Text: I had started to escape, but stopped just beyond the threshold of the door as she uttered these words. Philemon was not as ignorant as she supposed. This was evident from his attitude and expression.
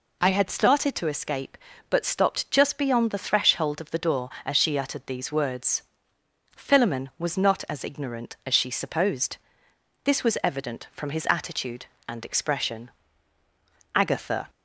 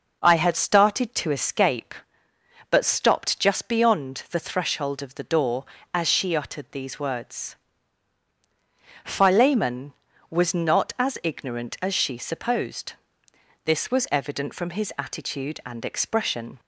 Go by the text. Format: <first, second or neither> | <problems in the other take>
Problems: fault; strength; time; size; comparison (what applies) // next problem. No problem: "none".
second | goes on to say "Agatha"; from 13.9 s on; 0.54 s long